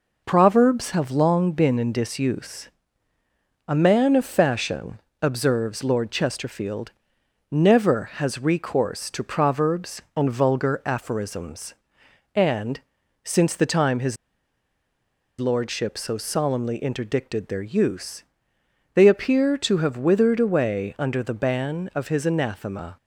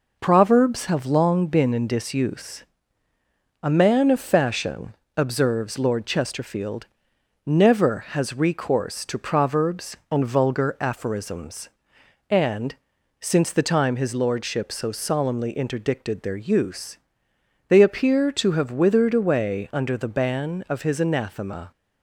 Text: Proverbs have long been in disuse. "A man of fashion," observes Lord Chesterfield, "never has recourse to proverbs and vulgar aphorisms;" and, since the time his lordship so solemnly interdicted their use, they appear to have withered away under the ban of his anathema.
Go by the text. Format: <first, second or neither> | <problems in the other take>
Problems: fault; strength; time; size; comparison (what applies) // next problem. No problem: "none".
second | pauses between "his" and "lordship"; at 14.1 s; 1.2 s long